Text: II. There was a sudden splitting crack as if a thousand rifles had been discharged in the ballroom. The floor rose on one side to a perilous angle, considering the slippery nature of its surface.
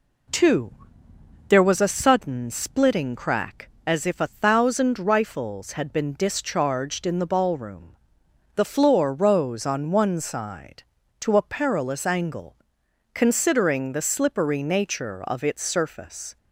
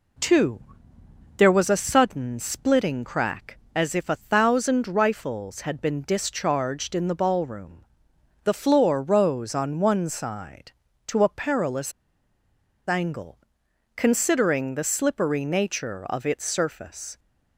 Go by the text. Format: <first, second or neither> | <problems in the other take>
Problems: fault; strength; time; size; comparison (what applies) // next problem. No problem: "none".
first | pauses between "perilous" and "angle"; noticeable; at 11.9 s; 0.97 s long